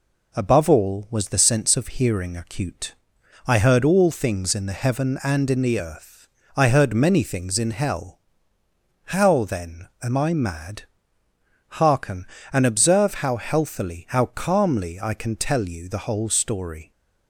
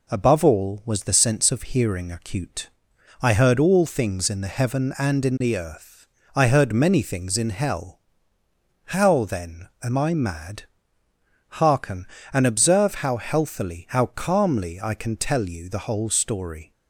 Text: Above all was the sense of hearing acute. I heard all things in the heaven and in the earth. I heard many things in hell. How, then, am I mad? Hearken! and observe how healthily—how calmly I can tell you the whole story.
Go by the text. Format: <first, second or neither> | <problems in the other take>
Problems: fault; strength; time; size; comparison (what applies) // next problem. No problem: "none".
neither | none